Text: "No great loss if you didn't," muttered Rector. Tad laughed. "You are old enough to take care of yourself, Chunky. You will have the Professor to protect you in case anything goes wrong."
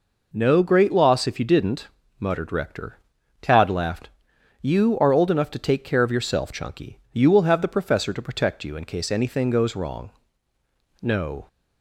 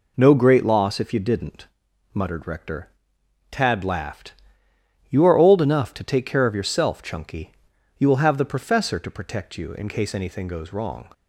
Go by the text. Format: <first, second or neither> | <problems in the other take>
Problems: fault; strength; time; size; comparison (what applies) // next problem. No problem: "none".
second | goes on to say "No"; slight; from 11.0 s on; 0.46 s long